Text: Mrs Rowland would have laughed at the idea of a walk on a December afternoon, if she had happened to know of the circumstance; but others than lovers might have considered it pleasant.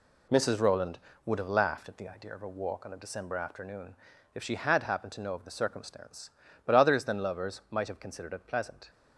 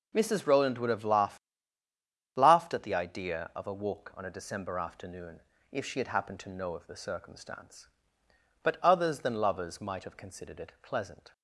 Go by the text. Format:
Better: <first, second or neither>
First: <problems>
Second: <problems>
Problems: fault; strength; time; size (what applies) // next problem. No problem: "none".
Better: first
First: none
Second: says "laughed" twice; at 2.3 s